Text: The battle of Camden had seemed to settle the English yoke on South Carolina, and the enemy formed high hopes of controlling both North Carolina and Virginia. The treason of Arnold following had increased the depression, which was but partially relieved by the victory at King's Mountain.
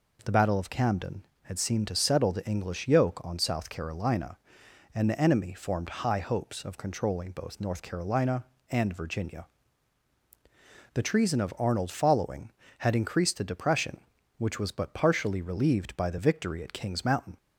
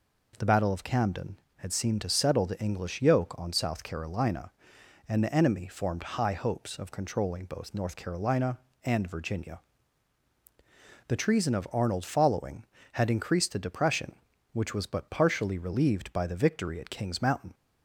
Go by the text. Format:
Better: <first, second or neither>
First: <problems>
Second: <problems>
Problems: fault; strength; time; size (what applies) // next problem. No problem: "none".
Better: neither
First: none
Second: none